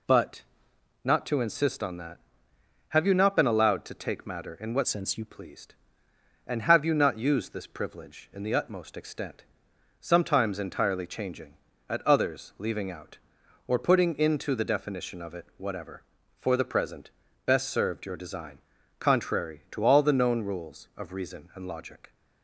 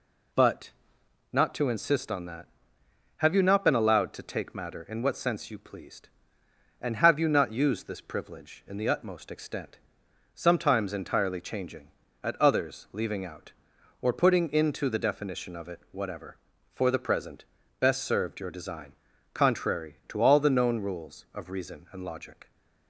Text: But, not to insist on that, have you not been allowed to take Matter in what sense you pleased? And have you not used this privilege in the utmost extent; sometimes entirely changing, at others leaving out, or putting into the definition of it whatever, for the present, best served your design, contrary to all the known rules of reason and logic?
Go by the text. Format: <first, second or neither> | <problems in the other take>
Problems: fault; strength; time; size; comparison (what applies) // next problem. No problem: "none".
second | changes voice from "sense" to "you"; from 4.8 to 5.2 s; 0.4 s long